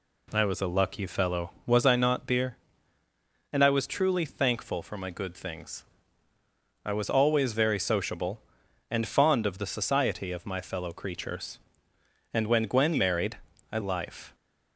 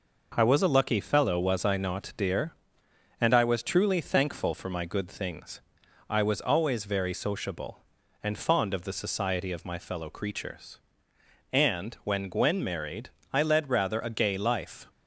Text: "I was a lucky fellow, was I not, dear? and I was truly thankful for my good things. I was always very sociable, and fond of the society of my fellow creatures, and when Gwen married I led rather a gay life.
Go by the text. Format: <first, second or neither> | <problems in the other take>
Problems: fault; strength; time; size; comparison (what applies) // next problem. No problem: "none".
second | pauses between "married" and "I"; slight; at 13.3 s; 0.32 s long; slight in the second // skips "led rather a gay"; at 13.7 s